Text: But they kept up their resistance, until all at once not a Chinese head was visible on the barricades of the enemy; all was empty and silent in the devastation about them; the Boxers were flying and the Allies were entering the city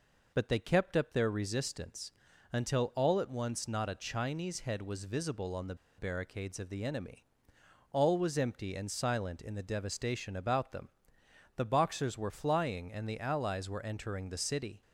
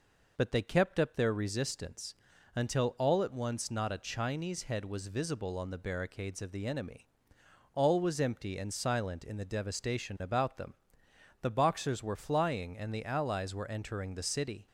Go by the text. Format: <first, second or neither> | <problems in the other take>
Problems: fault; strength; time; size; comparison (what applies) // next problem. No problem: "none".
second | pauses between "the" and "barricades"; slight; at 5.7 s; 0.23 s long